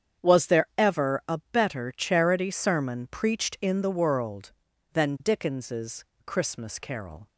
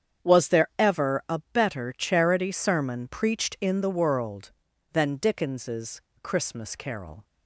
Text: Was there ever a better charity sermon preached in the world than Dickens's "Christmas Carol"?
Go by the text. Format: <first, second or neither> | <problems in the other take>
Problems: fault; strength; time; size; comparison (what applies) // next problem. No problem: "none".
neither | starts louder than the rest; strong; the same in both // pauses between "Dickens's" and "Christmas"; slight; the same in both